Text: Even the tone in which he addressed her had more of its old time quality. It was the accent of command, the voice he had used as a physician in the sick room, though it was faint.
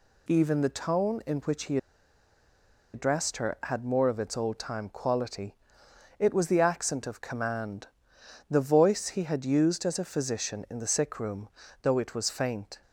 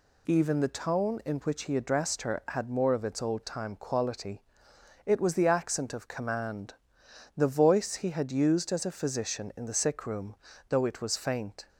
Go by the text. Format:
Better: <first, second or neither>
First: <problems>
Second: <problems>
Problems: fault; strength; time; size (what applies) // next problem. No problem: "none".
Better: second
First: pauses between "he" and "addressed"; at 1.7 s; 1.1 s long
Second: none